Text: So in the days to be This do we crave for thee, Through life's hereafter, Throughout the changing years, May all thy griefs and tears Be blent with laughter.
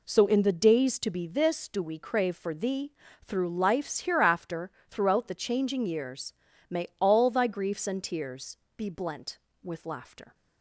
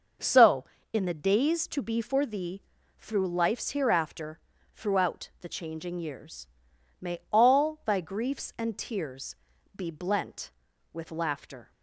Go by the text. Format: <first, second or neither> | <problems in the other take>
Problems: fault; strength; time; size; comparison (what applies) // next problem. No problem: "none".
first | starts louder than the rest; noticeable; until 1.4 s; 6 dB // skips "This do we crave"; at 2.0 s // pauses between "tears" and "Be"; at 9.3 s; 0.38 s long; slight in the first